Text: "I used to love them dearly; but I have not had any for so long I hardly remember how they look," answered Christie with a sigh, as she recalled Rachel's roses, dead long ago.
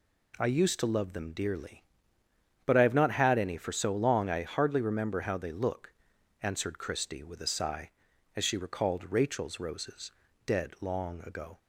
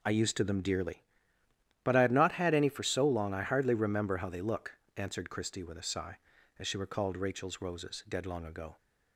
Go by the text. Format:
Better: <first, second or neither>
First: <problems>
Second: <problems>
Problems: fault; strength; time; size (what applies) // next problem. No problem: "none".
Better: first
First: none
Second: skips "love"; at 0.4 s